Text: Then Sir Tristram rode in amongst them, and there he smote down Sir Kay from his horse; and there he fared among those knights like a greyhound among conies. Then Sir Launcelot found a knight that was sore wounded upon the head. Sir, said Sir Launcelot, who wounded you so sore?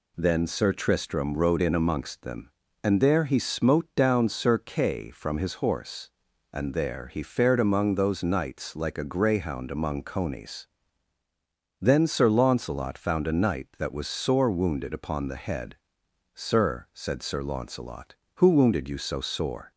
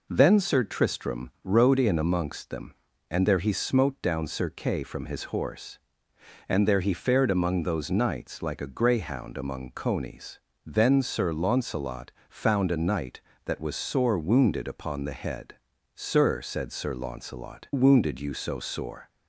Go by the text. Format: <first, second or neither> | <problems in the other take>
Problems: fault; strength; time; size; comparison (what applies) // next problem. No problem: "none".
first | pauses between "Launcelot" and "found"; slight; at 12.0 s; 0.20 s long // skips "who"; at 17.7 s